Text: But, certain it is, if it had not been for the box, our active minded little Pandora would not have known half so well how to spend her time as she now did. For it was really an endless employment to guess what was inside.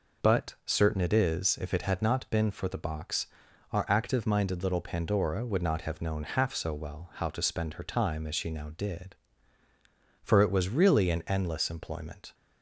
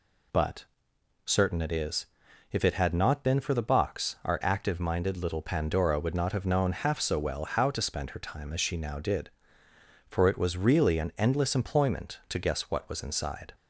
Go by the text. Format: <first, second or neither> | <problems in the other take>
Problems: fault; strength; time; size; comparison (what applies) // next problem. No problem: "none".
second | stops before "to guess what was inside"; at 12.3 s